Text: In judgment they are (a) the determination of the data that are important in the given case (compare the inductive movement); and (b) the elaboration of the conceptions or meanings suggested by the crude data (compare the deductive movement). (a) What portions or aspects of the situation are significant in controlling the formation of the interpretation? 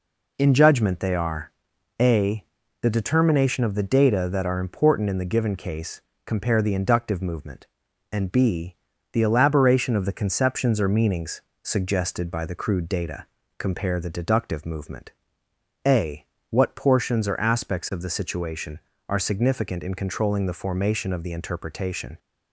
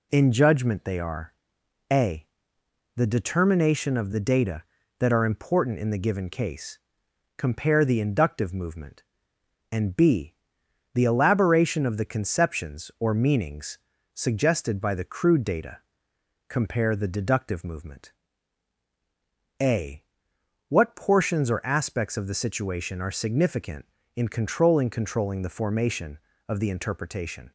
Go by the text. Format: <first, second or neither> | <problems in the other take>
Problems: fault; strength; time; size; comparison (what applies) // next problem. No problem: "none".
first | pauses between "are" and "a"; noticeable; at 1.3 s; 0.58 s long; noticeable in the first // pauses between "meanings" and "suggested"; slight; at 13.7 s; 0.36 s long; slight in the first // says "controlling" twice; at 24.8 s